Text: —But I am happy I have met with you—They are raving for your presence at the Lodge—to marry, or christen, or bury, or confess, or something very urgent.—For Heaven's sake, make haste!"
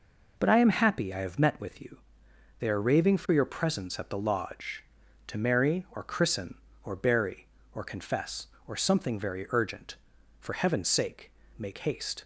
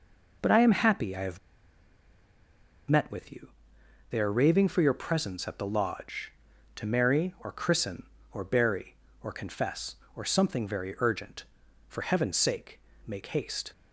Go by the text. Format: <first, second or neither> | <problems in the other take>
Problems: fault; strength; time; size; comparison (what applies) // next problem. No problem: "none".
first | pauses between "have" and "met"; strong; at 1.3 s; 1.5 s long